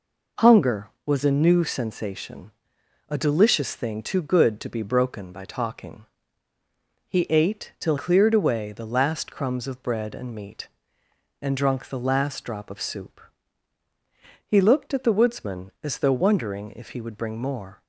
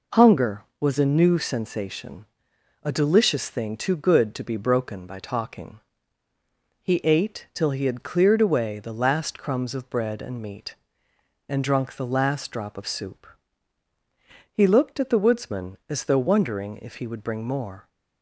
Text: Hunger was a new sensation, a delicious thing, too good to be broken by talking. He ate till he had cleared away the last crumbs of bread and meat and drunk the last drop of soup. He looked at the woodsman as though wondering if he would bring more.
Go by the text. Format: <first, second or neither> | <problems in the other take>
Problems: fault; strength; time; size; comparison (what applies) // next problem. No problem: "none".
second | skips "he had"; at 7.9 s